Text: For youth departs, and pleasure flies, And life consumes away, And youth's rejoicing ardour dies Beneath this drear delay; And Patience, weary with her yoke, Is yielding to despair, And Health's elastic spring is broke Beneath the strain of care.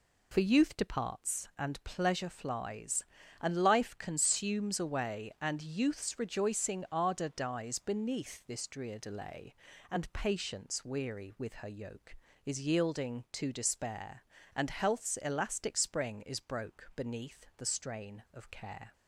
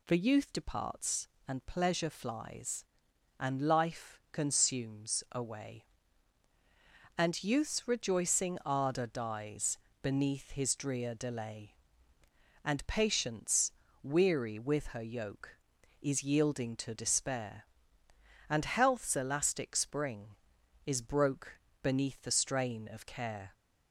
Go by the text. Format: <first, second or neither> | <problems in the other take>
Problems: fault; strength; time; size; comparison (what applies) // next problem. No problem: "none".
first | pauses between "dies" and "Beneath"; slight; at 9.7 s; 0.26 s long // says "his" for "this"; at 10.5 s // pauses between "broke" and "Beneath"; slight; at 21.5 s; 0.22 s long